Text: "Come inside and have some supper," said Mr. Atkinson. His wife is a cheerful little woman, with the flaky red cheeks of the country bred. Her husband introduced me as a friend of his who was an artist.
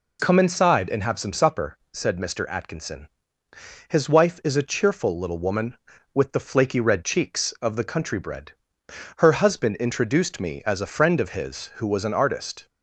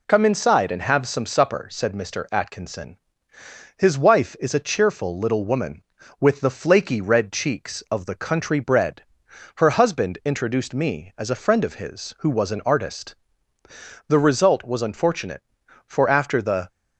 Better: first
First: none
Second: goes on to say "The result was unfortunate for after the"; strong; from 14.0 s on; 2.6 s long

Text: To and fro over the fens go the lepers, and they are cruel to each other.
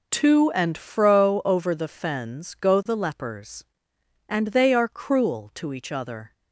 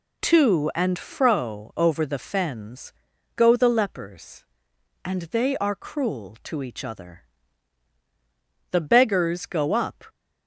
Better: first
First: none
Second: pauses between "fens" and "go"; at 2.9 s; 0.44 s long // goes on to say "The beggars go up"; from 8.7 s on; 1.3 s long

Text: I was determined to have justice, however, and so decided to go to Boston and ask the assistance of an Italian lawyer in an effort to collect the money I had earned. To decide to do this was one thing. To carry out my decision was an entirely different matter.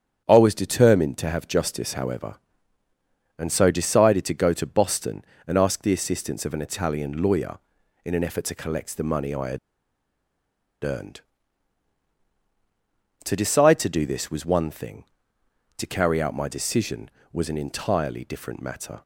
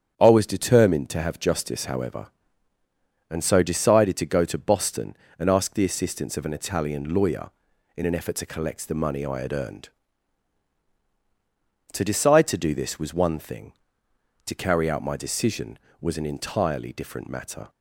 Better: second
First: starts louder than the rest; strong; until 1.2 s; 8.5 dB // pauses between "had" and "earned"; strong; at 9.5 s; 1.2 s long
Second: starts louder than the rest; strong; until 1.1 s; 8.5 dB

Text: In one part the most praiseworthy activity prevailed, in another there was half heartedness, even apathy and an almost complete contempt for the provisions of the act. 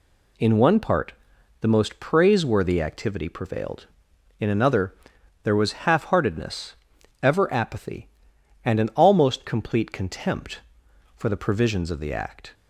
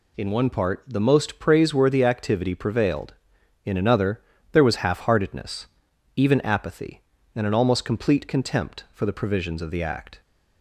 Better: second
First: pauses between "part" and "the"; noticeable; at 1.1 s; 0.48 s long // pauses between "another" and "there"; noticeable; at 4.9 s; 0.50 s long // says "ever" for "even"; at 7.2 s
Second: pauses between "another" and "there"; slight; at 4.2 s; 0.32 s long

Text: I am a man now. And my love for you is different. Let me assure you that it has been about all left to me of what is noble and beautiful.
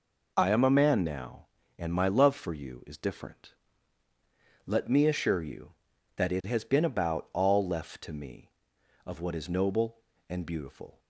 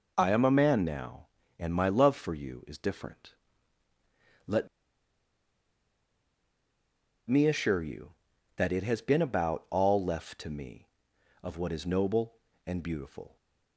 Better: first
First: none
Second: pauses between "Let" and "me"; strong; at 4.6 s; 2.6 s long

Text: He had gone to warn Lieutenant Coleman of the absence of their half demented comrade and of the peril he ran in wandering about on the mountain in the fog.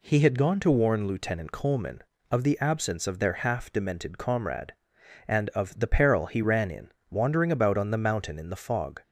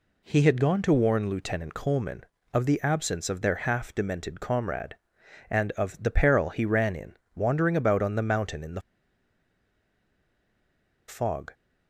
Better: first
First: pauses between "in" and "wandering"; slight; at 6.9 s; 0.18 s long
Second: pauses between "in" and "wandering"; slight; at 7.1 s; 0.18 s long // pauses between "the" and "fog"; strong; at 8.8 s; 2.2 s long

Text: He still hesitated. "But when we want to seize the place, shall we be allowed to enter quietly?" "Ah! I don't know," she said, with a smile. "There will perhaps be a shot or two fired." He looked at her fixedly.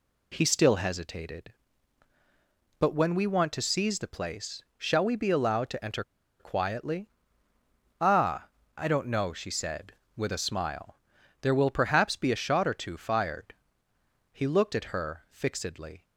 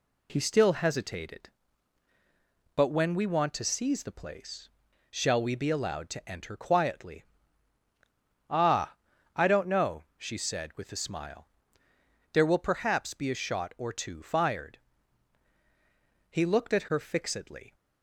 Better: second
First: pauses between "enter" and "quietly"; at 6.0 s; 0.37 s long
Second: none

